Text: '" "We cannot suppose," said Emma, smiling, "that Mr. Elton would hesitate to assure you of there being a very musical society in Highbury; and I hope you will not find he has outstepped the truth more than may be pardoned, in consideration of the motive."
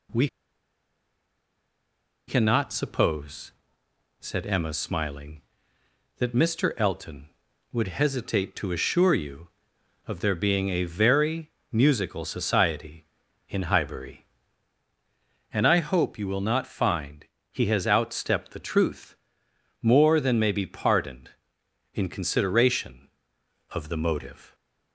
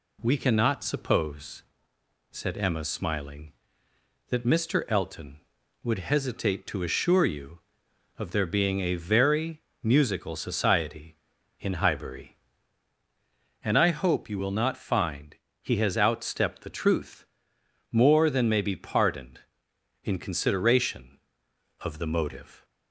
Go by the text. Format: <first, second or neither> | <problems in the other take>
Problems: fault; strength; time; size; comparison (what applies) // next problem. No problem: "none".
second | pauses between "We" and "cannot"; strong; at 0.2 s; 2.0 s long // pauses between "very" and "musical"; slight; at 11.5 s; 0.20 s long; slight in the second // pauses between "find" and "he"; slight; at 17.2 s; 0.24 s long; slight in the second // pauses between "truth" and "more"; noticeable; at 19.1 s; 0.68 s long; noticeable in the second